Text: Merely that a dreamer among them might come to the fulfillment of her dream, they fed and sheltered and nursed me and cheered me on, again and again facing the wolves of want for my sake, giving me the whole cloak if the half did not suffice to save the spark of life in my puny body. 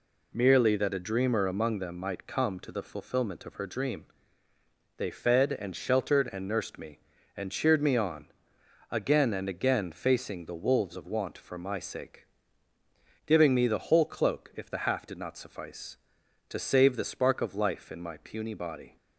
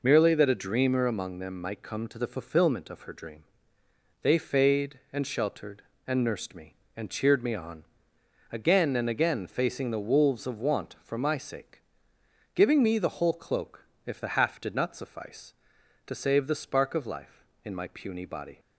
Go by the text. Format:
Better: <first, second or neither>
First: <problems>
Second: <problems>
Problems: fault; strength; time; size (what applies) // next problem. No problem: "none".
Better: first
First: none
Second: says "fade" for "fed"; at 4.3 s // pauses between "cloak" and "if"; slight; at 13.8 s; 0.20 s long